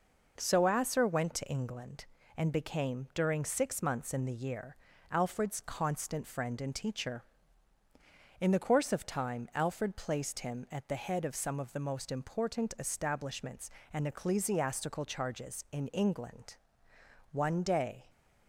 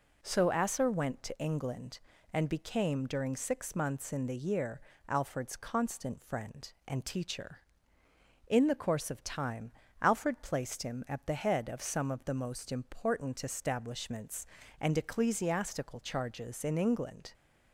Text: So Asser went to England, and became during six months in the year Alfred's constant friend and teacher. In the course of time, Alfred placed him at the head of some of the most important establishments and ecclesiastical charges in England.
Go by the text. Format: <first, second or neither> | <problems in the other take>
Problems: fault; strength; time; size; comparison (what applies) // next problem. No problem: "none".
second | pauses between "year" and "Alfred's"; slight; at 4.7 s; 0.34 s long; slight in the second // goes on to say "One day"; noticeable; from 17.3 s on; 0.78 s long